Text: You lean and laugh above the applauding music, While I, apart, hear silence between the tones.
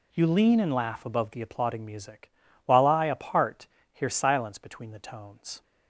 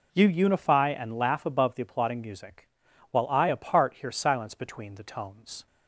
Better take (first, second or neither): first